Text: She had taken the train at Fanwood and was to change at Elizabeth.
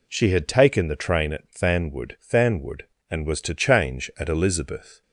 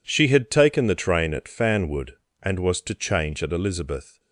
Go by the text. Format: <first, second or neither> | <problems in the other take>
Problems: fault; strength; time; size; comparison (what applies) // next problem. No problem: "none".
second | says "Fanwood" twice; at 2.2 s